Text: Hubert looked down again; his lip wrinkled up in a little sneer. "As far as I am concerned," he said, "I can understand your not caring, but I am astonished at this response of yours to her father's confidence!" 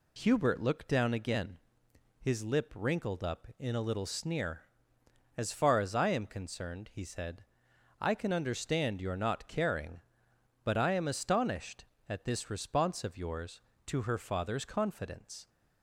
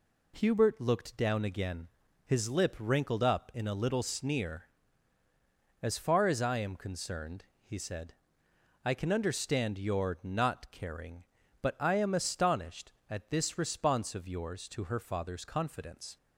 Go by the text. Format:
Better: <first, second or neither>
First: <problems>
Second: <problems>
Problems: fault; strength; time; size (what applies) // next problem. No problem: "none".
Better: neither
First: none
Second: none